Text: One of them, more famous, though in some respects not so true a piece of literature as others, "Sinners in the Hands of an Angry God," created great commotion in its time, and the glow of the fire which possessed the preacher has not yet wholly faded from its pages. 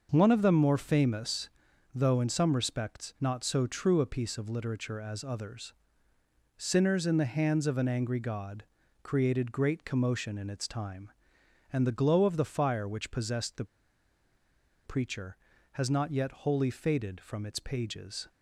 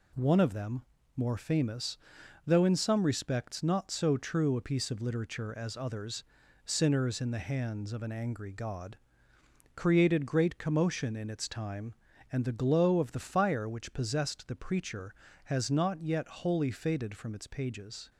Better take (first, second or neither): second